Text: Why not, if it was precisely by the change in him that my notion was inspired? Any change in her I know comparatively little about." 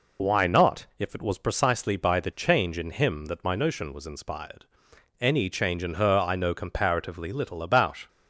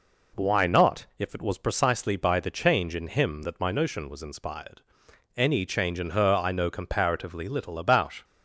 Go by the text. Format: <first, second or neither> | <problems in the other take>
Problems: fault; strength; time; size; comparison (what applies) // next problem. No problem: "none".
second | loses the start of "Why"; at 0.1 s; 65 ms